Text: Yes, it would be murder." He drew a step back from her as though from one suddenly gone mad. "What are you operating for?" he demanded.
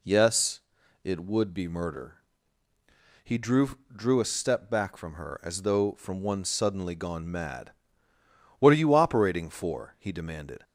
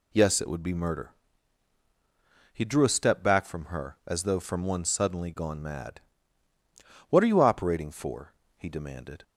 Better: second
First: says "drew" twice; at 3.9 s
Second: none

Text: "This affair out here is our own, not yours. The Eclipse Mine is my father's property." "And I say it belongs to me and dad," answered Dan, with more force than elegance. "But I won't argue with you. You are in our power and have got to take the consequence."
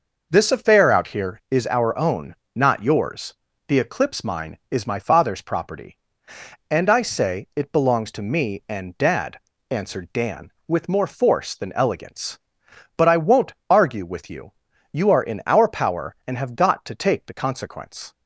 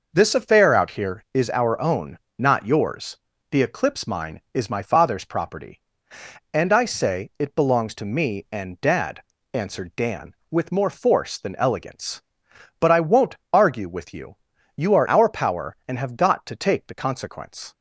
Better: first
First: pauses between "won't" and "argue"; slight; at 13.5 s; 0.16 s long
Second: pauses between "won't" and "argue"; slight; at 13.3 s; 0.16 s long // skips "in"; at 15.0 s

